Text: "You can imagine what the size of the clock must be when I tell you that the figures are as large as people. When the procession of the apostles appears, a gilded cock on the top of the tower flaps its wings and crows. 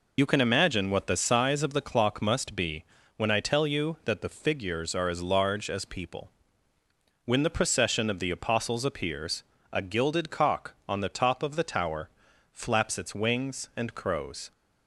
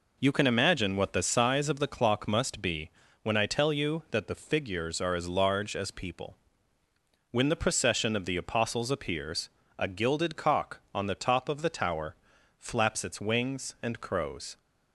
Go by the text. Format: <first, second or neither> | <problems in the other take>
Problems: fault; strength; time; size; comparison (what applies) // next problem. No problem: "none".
second | loses the start of "You"; at 0.1 s; 45 ms // pauses between "be" and "when"; slight; at 2.8 s; 0.32 s long; slight in the second // pauses between "tower" and "flaps"; at 12.0 s; 0.42 s long; also in the second